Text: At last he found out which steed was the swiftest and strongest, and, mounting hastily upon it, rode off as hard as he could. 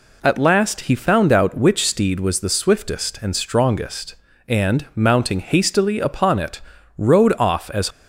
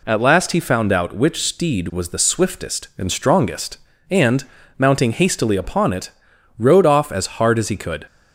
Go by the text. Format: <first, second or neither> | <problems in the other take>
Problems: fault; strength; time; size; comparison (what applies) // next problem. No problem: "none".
second | stops before "hard as he could"; at 7.9 s